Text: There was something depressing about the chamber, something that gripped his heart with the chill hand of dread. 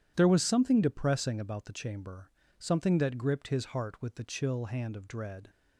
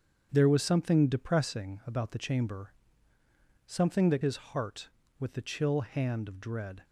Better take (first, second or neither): first